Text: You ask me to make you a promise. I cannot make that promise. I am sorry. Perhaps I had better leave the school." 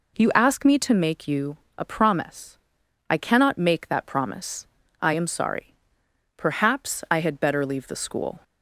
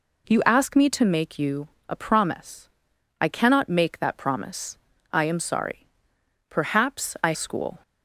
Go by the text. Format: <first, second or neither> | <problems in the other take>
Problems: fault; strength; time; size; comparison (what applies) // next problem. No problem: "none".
first | pauses between "you" and "a"; slight; at 1.6 s; 0.20 s long; slight in the first // skips "had better leave the"; at 7.3 s